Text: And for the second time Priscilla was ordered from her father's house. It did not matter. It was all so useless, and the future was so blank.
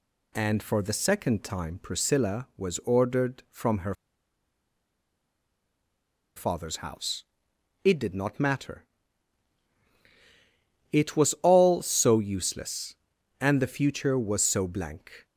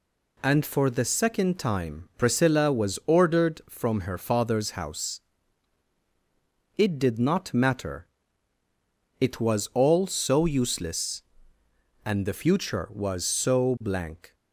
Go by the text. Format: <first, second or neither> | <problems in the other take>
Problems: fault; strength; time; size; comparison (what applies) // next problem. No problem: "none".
second | pauses between "her" and "father's"; strong; at 3.9 s; 2.4 s long